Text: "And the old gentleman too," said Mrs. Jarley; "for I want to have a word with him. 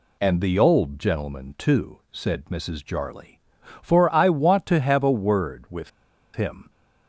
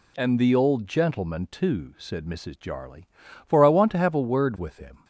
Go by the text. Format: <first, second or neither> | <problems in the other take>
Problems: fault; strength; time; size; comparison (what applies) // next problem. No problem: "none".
second | pauses between "with" and "him"; at 5.8 s; 0.45 s long